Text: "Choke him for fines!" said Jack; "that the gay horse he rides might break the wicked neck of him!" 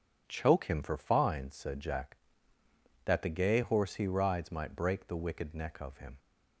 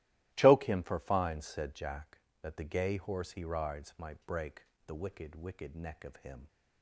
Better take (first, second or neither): first